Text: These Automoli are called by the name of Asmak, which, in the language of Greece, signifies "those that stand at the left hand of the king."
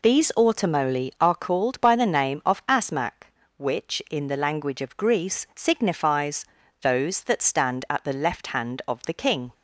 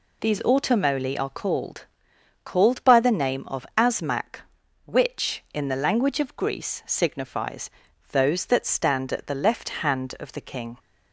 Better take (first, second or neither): first